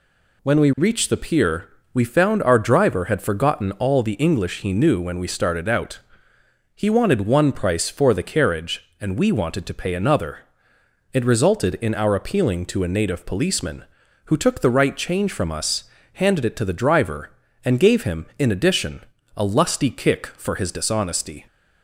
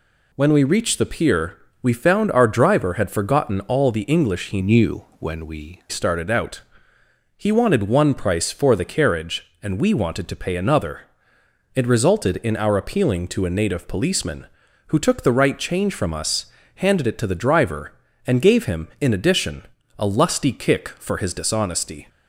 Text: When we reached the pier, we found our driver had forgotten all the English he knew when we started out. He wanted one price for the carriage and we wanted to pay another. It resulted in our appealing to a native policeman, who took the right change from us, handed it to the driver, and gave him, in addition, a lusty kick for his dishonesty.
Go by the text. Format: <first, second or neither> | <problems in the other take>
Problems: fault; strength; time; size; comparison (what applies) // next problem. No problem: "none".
first | changes voice from "knew" to "we"; from 4.6 to 5.8 s; 1.2 s long // pauses between "knew" and "when"; slight; at 5.0 s; 0.16 s long